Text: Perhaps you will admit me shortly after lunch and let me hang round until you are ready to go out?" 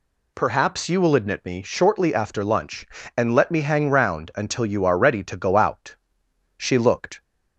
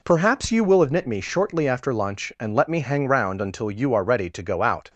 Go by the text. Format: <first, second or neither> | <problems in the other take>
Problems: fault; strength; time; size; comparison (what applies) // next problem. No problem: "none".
second | goes on to say "She looked"; noticeable; from 6.5 s on; 0.64 s long